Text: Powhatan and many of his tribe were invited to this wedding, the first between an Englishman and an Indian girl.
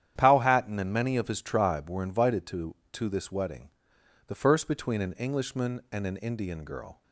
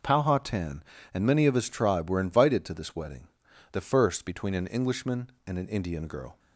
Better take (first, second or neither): second